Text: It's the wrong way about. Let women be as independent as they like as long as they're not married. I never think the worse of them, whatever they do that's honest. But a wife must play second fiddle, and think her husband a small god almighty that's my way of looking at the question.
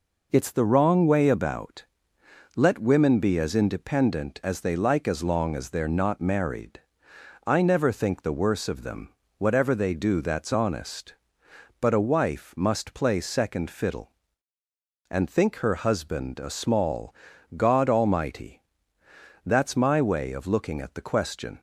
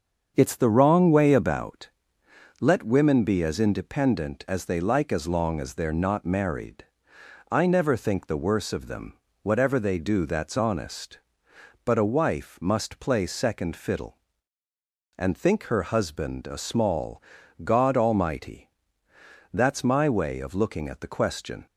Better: first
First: pauses between "small" and "god"; at 17.1 s; 0.42 s long // pauses between "almighty" and "that's"; noticeable; at 18.5 s; 0.86 s long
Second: starts louder than the rest; until 1.7 s; 7 dB // pauses between "small" and "god"; at 17.2 s; 0.42 s long // pauses between "almighty" and "that's"; noticeable; at 18.6 s; 0.86 s long

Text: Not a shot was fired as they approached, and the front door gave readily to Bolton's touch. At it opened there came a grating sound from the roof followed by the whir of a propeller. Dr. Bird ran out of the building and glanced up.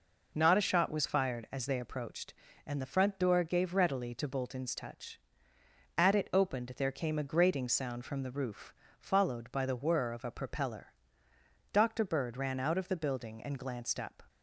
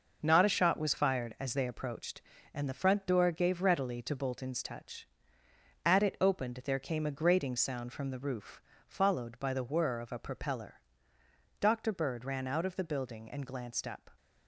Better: first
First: pauses between "roof" and "followed"; slight; at 8.7 s; 0.28 s long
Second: gets quieter; throughout; 7 dB // pauses between "roof" and "followed"; slight; at 8.6 s; 0.28 s long

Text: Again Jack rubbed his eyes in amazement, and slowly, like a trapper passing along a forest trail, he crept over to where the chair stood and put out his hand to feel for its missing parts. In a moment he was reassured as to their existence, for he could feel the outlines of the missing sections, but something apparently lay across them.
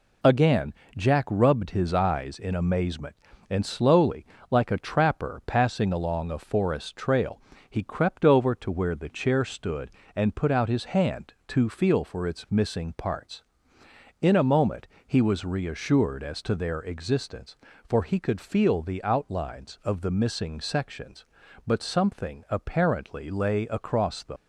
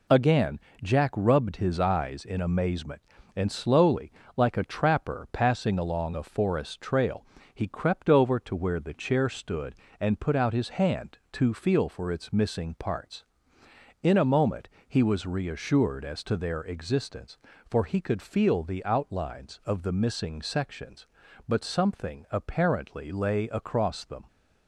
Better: second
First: pauses between "Again" and "Jack"; slight; at 0.7 s; 0.22 s long // pauses between "moment" and "he"; slight; at 14.8 s; 0.20 s long // leaves "them" unfinished; at 24.3 s; 90 ms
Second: pauses between "Again" and "Jack"; slight; at 0.5 s; 0.22 s long // pauses between "moment" and "he"; slight; at 14.6 s; 0.20 s long

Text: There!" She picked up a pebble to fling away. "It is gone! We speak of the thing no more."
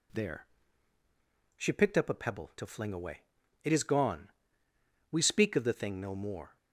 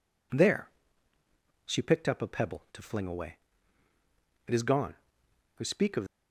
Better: first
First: none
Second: stops before "the thing no more"; at 6.0 s

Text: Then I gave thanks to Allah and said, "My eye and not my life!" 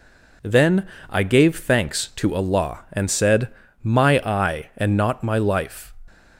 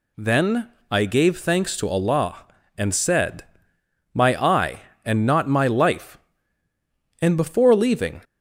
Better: first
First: pauses between "Then" and "I"; slight; at 0.8 s; 0.22 s long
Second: pauses between "Then" and "I"; slight; at 0.7 s; 0.20 s long // goes on to say "and before leaving"; noticeable; from 7.2 s on; 0.98 s long

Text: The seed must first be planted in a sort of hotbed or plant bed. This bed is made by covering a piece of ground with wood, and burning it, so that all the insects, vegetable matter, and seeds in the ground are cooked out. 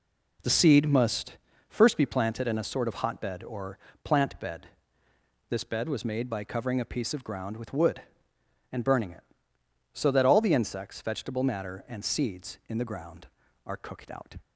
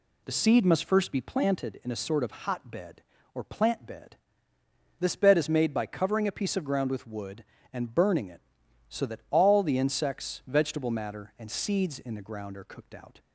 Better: second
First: pauses between "must" and "first"; slight; at 1.3 s; 0.32 s long // pauses between "or" and "plant"; slight; at 3.7 s; 0.26 s long // says "was" for "is"; at 5.8 s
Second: none

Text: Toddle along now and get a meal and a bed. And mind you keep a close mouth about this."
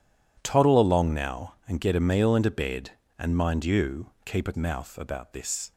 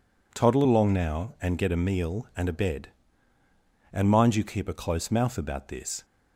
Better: second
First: skips "close"; at 4.5 s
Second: none

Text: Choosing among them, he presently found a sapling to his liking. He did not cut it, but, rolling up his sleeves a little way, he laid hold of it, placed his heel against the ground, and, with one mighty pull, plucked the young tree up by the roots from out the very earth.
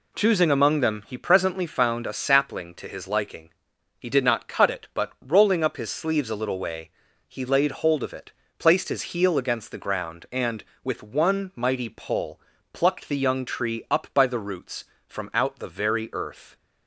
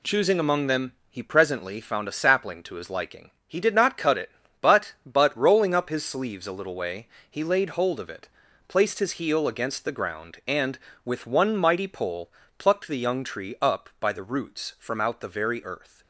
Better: first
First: none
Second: says "but" twice; at 5.0 s

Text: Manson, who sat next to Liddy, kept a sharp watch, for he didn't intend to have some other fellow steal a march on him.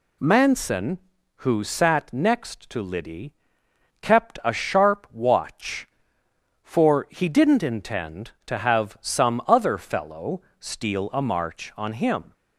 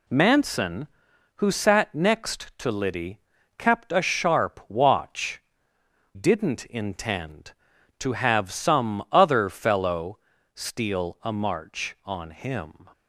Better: first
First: pauses between "fellow" and "steal"; slight; at 10.4 s; 0.18 s long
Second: skips "for he"; at 5.7 s // pauses between "fellow" and "steal"; slight; at 10.1 s; 0.36 s long

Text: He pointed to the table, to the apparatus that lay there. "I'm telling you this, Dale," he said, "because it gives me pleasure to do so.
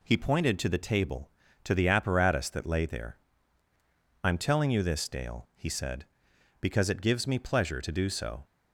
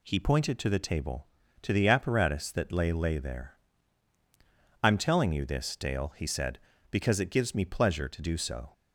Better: first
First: none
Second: says "lay" twice; at 2.9 s

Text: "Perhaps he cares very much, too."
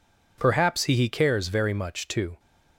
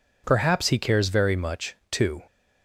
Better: second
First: says "he" twice; at 0.9 s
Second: none

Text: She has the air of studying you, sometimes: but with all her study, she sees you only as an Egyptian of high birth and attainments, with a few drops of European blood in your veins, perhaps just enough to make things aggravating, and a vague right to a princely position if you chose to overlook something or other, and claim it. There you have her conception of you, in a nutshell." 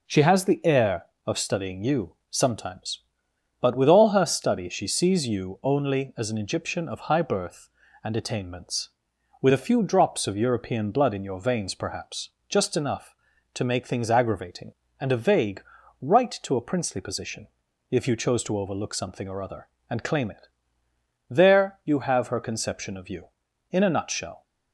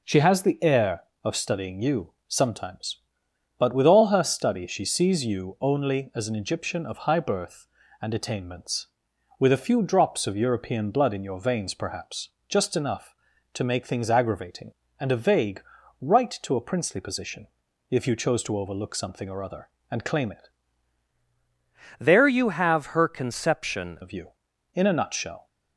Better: first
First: pauses between "perhaps" and "just"; slight; at 12.2 s; 0.22 s long // pauses between "vague" and "right"; at 15.6 s; 0.40 s long // pauses between "position" and "if"; at 17.4 s; 0.42 s long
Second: pauses between "perhaps" and "just"; slight; at 12.2 s; 0.22 s long // pauses between "vague" and "right"; at 15.6 s; 0.40 s long // pauses between "position" and "if"; at 17.4 s; 0.42 s long // changes voice from "There" to "conception"; from 21.9 to 23.9 s; 2.0 s long

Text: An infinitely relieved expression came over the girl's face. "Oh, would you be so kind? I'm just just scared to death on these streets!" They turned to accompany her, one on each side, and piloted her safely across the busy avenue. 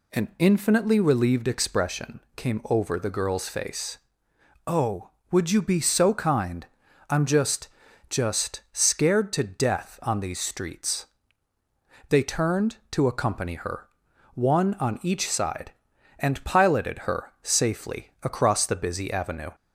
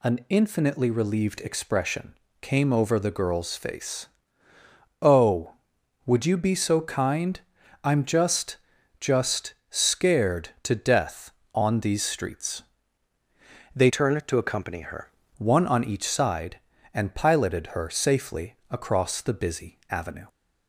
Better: first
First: pauses between "expression" and "came"; slight; at 2.1 s; 0.16 s long // pauses between "just" and "just"; at 7.6 s; 0.40 s long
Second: pauses between "expression" and "came"; slight; at 2.1 s; 0.26 s long // pauses between "just" and "just"; at 8.5 s; 0.42 s long // pauses between "just" and "scared"; slight; at 9.5 s; 0.16 s long // changes voice from "turned" to "her"; from 13.8 to 15.1 s; 1.3 s long // pauses between "safely" and "across"; slight; at 18.5 s; 0.16 s long

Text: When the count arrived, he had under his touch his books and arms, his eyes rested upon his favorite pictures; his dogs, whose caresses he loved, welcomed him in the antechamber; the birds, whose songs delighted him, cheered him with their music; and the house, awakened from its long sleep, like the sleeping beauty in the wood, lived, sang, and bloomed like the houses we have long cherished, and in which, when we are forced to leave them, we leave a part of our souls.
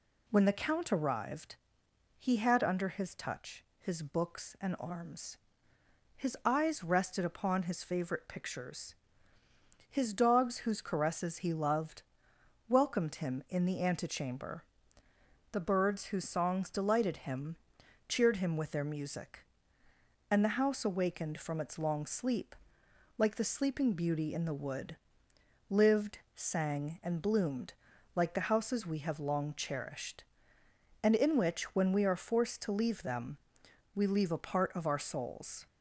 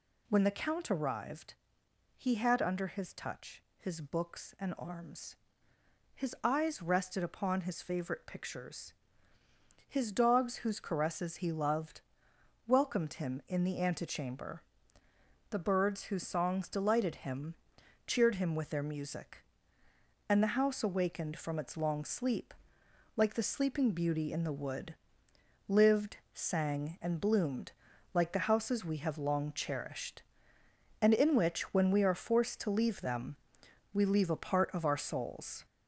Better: first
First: pauses between "touch" and "his"; slight; at 3.6 s; 0.16 s long // pauses between "bloomed" and "like"; at 27.7 s; 0.42 s long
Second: gets louder; noticeable; throughout; 5 dB // pauses between "touch" and "his"; slight; at 3.6 s; 0.16 s long // pauses between "bloomed" and "like"; at 27.7 s; 0.42 s long

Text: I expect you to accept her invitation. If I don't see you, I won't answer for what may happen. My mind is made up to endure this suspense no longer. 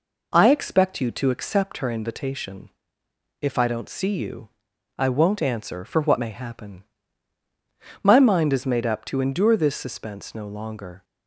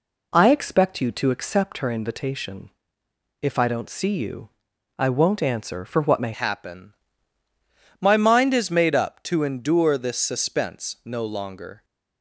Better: first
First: none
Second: changes voice at "happen"; from 6.3 s on; 5.5 s long

